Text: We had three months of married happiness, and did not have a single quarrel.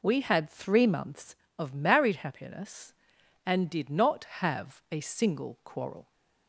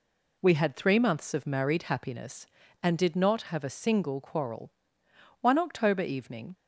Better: first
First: none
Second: goes on to say "One October evening"; noticeable; from 5.4 s on; 1.1 s long

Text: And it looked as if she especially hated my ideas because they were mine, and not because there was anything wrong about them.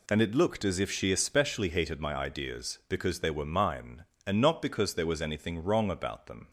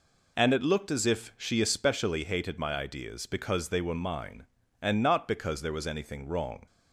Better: first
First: none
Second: stops before "about them"; at 6.6 s

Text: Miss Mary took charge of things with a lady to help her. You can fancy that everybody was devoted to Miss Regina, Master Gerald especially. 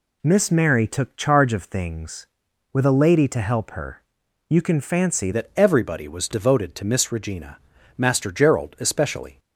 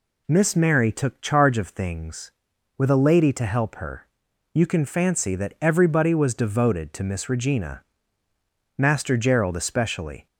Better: second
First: changes voice at "that"; from 5.3 s on; 4.0 s long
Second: none

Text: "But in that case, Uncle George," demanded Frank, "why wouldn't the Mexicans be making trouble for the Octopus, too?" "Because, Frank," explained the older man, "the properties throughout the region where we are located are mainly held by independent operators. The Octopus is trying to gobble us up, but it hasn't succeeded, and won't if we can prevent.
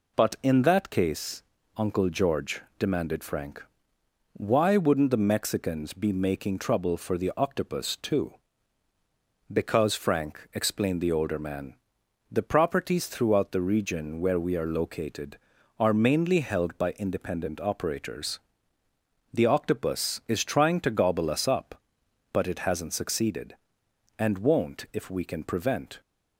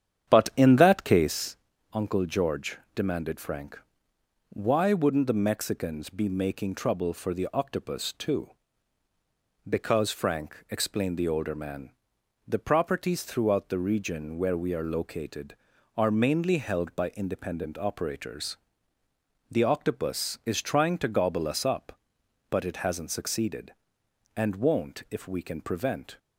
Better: first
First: none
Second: starts louder than the rest; strong; until 1.7 s; 9 dB

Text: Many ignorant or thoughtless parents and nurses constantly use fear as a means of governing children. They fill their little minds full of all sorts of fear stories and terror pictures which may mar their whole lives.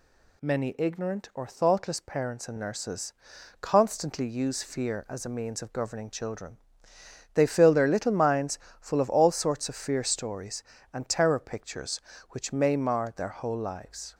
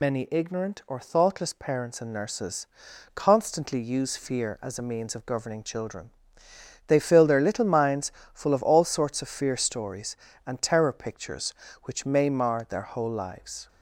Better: first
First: pauses between "nurses" and "constantly"; noticeable; at 3.1 s; 0.50 s long // pauses between "minds" and "full"; slight; at 8.5 s; 0.22 s long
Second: loses the start of "Many"; at 0.0 s; 70 ms // pauses between "nurses" and "constantly"; noticeable; at 2.6 s; 0.50 s long // pauses between "minds" and "full"; slight; at 8.1 s; 0.22 s long

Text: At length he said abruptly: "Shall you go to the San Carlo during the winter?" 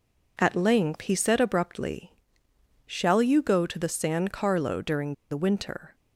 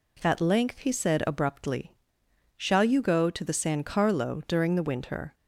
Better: second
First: pauses between "during" and "the"; slight; at 5.1 s; 0.16 s long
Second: none

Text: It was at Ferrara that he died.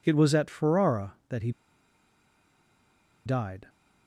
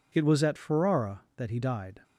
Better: second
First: pauses between "he" and "died"; strong; at 1.5 s; 1.7 s long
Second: none

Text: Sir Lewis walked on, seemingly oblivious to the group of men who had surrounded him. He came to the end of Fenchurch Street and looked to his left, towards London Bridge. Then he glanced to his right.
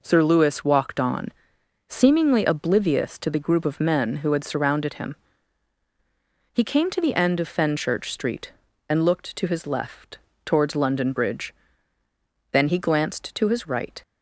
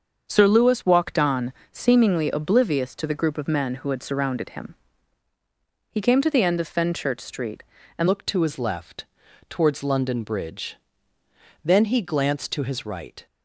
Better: first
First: none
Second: starts louder than the rest; until 1.2 s; 7 dB // changes voice at "looked"; from 8.0 s on; 5.2 s long

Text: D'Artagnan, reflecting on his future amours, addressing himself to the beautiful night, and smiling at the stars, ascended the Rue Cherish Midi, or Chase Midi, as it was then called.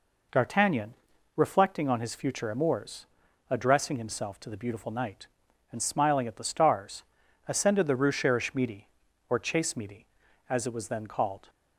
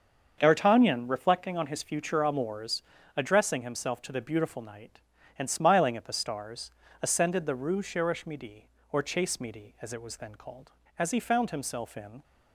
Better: first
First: none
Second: starts louder than the rest; until 1.3 s; 7 dB // goes on to say "As he found himself in"; noticeable; from 10.9 s on; 1.2 s long

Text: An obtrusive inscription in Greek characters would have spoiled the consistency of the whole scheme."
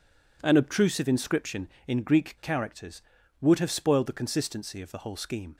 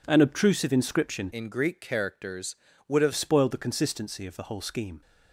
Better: first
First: none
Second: changes voice from "in" to "have"; from 1.3 to 3.1 s; 1.8 s long

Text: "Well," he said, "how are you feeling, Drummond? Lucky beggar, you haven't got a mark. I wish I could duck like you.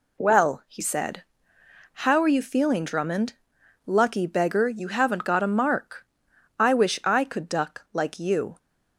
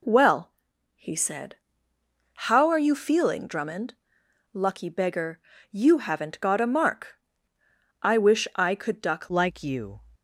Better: first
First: none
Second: changes voice at "like"; from 9.2 s on; 0.8 s long

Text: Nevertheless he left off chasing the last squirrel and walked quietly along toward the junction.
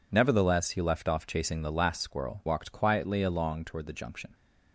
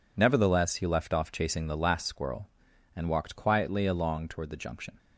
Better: second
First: skips "and"; at 2.4 s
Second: none

